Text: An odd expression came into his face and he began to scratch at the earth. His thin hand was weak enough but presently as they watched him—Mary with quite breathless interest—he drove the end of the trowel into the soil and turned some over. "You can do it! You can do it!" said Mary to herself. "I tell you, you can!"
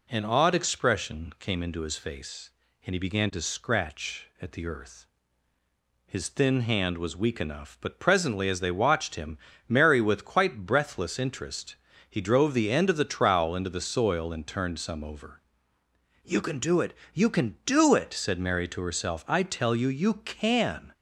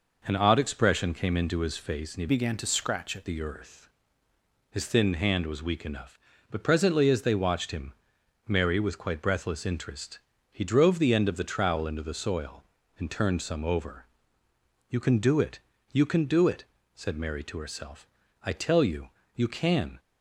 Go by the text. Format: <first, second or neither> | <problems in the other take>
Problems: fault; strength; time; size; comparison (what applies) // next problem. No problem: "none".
first | changes voice from "began" to "at"; from 2.2 to 3.2 s; 1.0 s long